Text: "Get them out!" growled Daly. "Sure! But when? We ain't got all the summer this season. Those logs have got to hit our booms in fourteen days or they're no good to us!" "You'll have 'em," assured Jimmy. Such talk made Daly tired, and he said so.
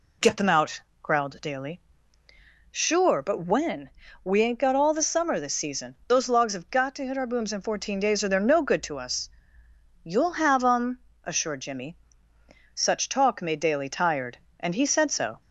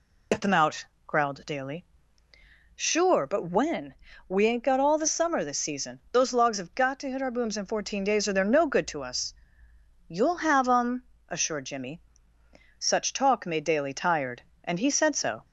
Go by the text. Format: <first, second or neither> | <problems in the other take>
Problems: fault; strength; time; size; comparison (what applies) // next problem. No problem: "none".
first | loses the start of "Get"; at 0.3 s; 65 ms